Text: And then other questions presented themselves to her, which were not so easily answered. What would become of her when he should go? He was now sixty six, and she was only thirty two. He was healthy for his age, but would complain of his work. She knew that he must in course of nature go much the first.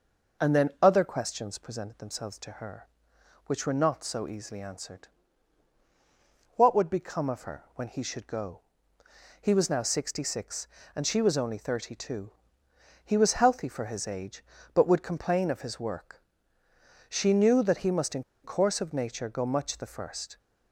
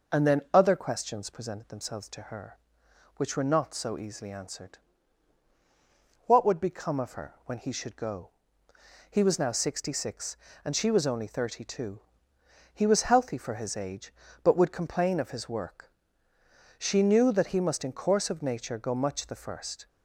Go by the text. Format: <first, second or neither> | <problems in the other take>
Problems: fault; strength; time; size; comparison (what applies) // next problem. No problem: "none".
second | pauses between "in" and "course"; slight; at 18.2 s; 0.21 s long